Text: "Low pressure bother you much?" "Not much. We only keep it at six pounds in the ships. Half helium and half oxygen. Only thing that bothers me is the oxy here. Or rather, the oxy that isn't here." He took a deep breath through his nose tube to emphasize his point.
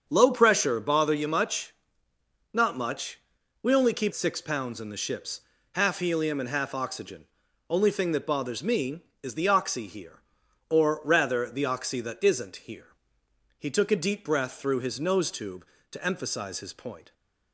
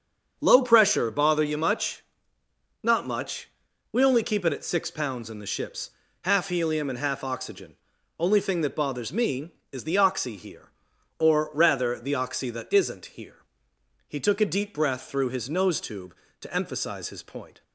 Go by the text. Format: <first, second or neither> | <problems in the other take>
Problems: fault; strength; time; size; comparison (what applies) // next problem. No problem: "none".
second | starts louder than the rest; strong; until 1.0 s; 7 dB; strong in the second // skips "it at"; at 4.1 s